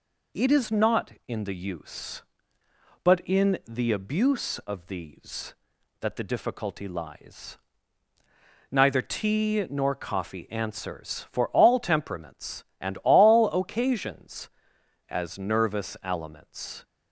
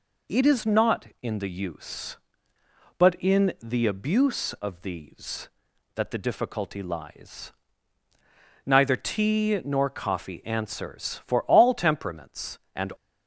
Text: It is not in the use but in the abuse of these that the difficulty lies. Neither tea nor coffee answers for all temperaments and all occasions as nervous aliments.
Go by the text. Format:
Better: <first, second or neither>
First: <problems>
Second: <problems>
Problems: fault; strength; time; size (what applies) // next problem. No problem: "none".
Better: first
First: none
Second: stops before "all occasions as nervous aliments"; at 12.9 s